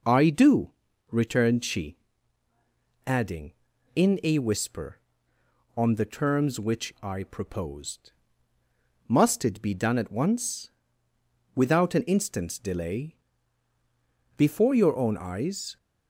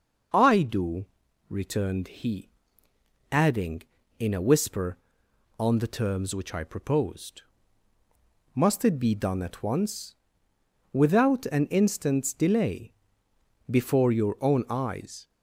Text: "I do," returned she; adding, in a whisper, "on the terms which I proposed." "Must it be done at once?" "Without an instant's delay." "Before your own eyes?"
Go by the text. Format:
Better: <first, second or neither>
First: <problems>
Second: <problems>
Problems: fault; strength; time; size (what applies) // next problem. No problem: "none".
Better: first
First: none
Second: says "he" for "she"; at 2.0 s